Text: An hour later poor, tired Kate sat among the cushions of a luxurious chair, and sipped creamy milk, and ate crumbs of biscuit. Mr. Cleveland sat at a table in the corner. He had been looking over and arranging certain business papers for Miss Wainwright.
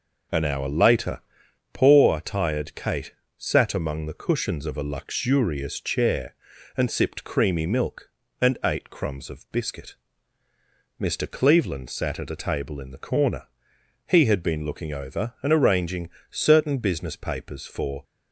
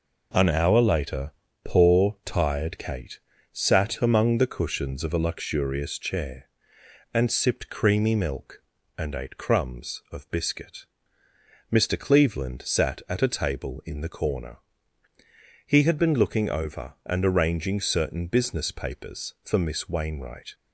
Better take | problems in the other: second | pauses between "later" and "poor"; noticeable; at 1.2 s; 0.52 s long; slight in the second // pauses between "Kate" and "sat"; slight; at 3.1 s; 0.24 s long; slight in the second // pauses between "arranging" and "certain"; slight; at 16.0 s; 0.22 s long // stops before "Miss Wainwright"; at 18.0 s

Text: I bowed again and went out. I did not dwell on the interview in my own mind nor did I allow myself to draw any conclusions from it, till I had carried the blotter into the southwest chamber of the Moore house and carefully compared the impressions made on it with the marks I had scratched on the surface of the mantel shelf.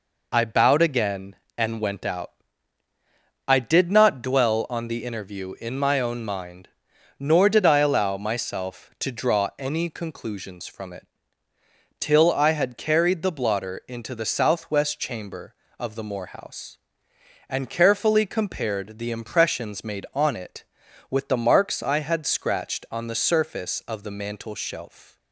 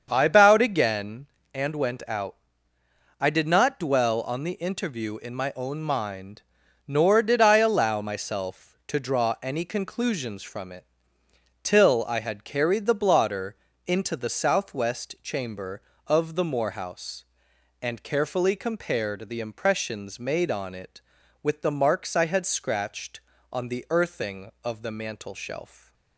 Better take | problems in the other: first | starts louder than the rest; strong; until 1.1 s; 7 dB // pauses between "mind" and "nor"; noticeable; at 6.4 s; 0.46 s long; noticeable in the first // pauses between "blotter" and "into"; slight; at 13.5 s; 0.30 s long // says "earthing" for "surface"; at 23.9 s // stays silent after the last word; slight; from 25.6 s on; 0.5 s long

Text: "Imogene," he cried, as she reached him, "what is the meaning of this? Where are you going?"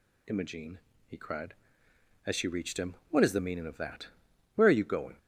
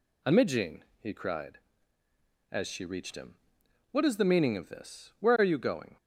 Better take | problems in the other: second | says "that" for "this"; at 3.7 s

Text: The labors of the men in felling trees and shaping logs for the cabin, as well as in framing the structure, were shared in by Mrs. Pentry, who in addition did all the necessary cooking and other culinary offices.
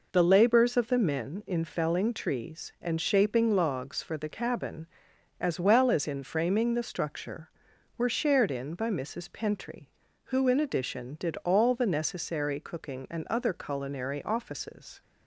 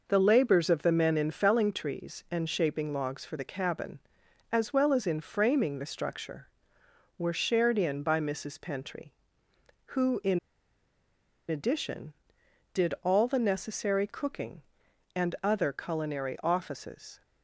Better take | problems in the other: first | pauses between "in" and "addition"; at 10.3 s; 1.1 s long

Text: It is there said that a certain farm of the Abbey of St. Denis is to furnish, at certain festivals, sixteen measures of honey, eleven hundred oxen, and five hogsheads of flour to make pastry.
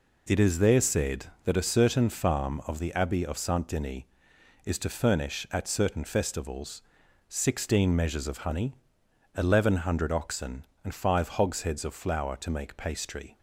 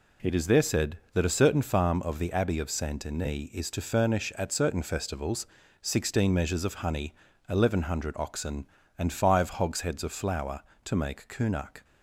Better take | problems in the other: first | says "kunak" for "pastry"; at 11.2 s

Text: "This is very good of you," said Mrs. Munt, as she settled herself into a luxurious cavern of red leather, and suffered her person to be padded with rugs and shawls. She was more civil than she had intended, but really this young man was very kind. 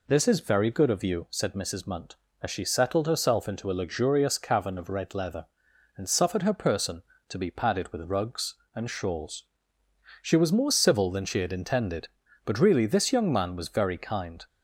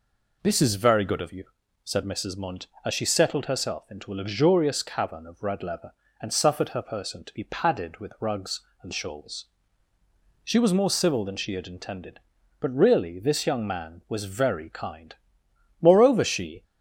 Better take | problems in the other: first | goes on to say "Moreover she"; noticeable; from 15.8 s on; 0.82 s long

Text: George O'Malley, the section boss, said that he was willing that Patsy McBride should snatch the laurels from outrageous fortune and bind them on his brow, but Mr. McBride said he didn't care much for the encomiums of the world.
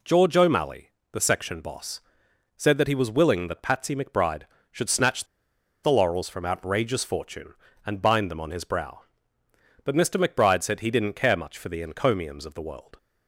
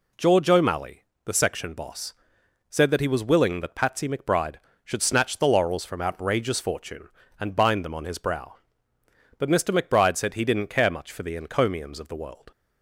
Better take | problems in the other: second | pauses between "snatch" and "the"; noticeable; at 5.2 s; 0.57 s long

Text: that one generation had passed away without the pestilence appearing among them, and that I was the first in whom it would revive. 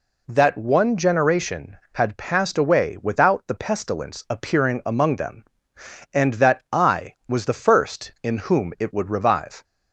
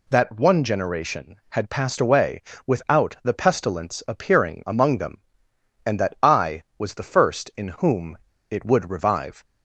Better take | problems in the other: first | pauses between "away" and "without"; slight; at 2.4 s; 0.24 s long // pauses between "whom" and "it"; slight; at 8.1 s; 0.31 s long

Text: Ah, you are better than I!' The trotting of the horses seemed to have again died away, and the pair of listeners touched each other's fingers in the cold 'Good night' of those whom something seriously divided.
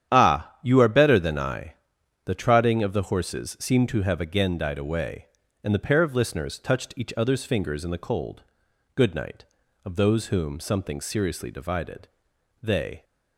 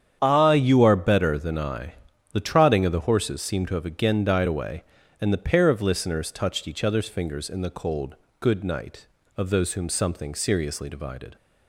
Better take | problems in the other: second | starts louder than the rest; strong; until 1.1 s; 10 dB; strong in the second // pauses between "cold" and "Good"; noticeable; at 8.4 s; 0.52 s long; slight in the second // goes on to say "They"; slight; from 12.6 s on; 0.42 s long

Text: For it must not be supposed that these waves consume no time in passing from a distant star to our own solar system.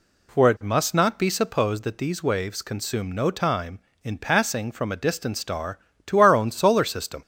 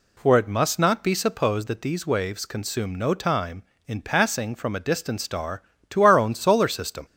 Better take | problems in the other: neither | none

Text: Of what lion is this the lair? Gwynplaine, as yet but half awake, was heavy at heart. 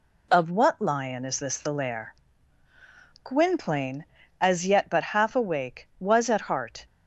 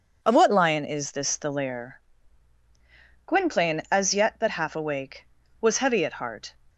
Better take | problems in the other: second | skips "heavy"; at 6.2 s

